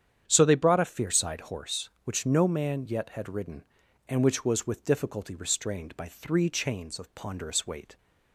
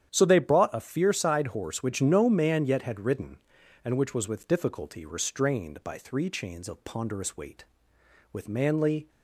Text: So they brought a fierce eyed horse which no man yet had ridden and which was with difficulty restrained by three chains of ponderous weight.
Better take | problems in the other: first | starts louder than the rest; strong; until 1.1 s; 9.5 dB; strong in the first // goes on to say "With manly"; noticeable; from 8.3 s on; 0.76 s long

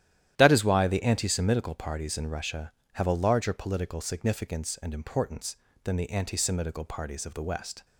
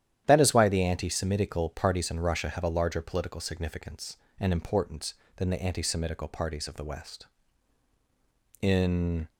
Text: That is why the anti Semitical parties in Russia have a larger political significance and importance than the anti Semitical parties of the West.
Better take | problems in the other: first | starts louder than the rest; strong; until 1.2 s; 11 dB; strong in the first // goes on to say "In"; noticeable; from 8.6 s on; 0.68 s long

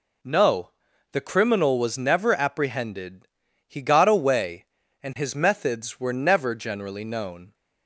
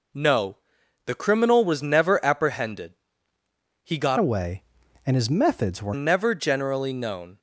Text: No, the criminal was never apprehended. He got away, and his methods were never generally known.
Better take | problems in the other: first | changes voice from "away" to "were"; from 4.1 to 5.9 s; 1.8 s long

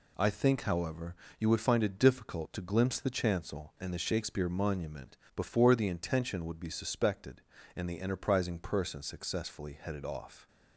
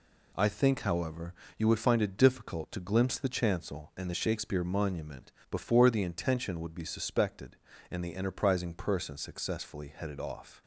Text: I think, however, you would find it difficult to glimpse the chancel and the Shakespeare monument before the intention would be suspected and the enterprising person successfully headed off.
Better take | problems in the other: neither | pauses between "monument" and "before"; slight; the same in both

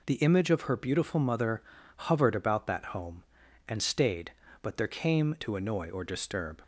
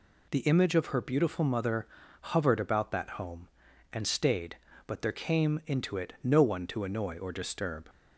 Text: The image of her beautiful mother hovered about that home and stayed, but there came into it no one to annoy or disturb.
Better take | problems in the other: second | pauses between "mother" and "hovered"; slight; at 1.6 s; 0.34 s long; slight in the second // skips "into it no one"; at 5.3 s

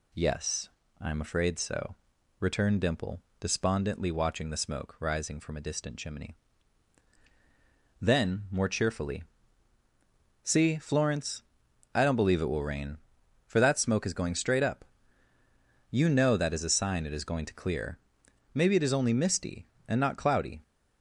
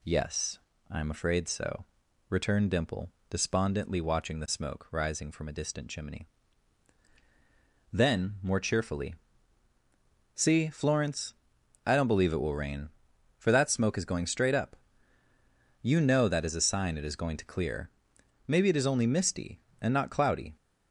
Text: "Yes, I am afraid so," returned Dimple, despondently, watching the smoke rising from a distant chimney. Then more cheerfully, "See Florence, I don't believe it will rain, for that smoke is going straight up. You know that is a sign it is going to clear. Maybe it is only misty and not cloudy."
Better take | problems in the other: neither | none

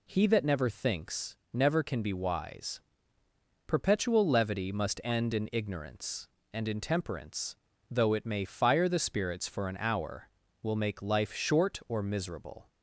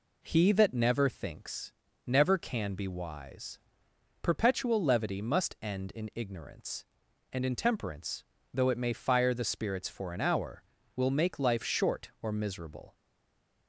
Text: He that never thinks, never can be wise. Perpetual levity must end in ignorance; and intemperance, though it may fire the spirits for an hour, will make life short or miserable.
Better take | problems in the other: first | stays silent after the last word; slight; from 12.9 s on; 0.7 s long

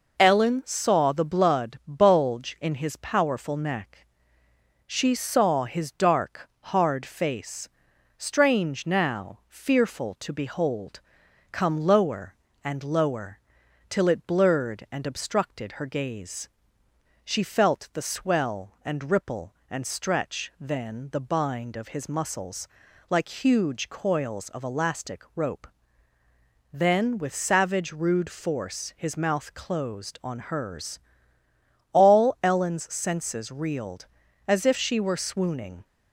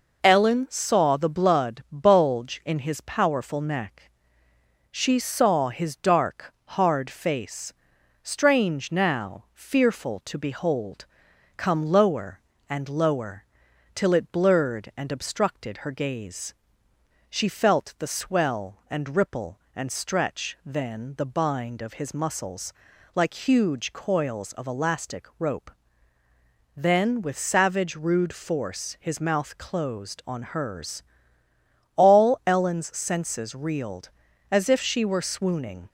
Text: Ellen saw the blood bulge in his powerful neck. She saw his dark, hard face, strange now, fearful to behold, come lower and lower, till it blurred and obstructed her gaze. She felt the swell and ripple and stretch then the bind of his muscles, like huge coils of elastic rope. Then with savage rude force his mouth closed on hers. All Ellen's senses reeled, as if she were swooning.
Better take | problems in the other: neither | none

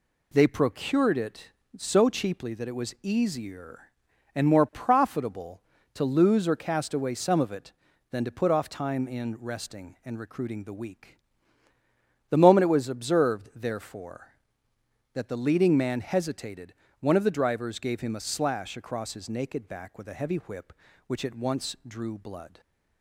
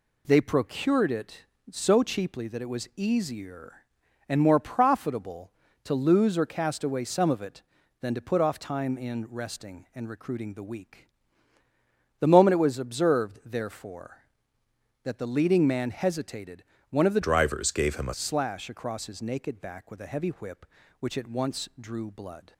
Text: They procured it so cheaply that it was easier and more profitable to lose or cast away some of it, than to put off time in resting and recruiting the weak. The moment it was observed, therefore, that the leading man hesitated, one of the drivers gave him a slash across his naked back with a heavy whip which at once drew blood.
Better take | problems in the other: first | changes voice from "drivers" to "a"; from 17.2 to 18.1 s; 0.9 s long

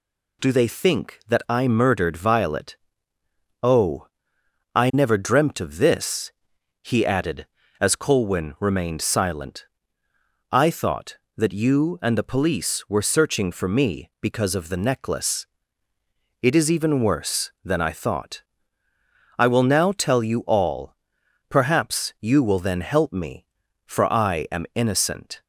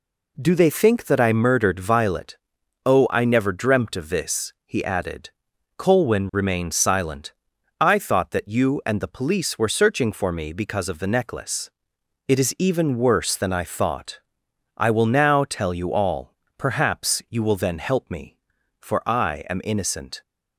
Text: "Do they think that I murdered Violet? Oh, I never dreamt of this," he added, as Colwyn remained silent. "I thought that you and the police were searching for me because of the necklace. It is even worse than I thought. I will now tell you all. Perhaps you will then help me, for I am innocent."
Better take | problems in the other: first | skips "as"; at 5.5 s

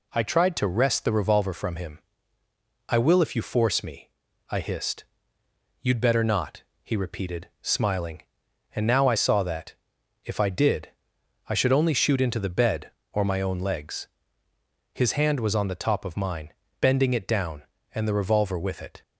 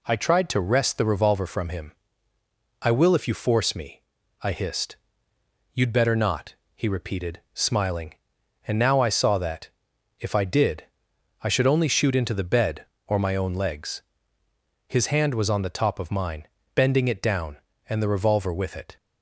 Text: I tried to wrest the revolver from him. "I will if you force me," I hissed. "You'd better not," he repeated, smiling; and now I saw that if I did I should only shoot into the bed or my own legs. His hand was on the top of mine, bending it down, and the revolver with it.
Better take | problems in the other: neither | pauses between "that" and "if"; noticeable; the same in both // pauses between "did" and "I"; noticeable; the same in both

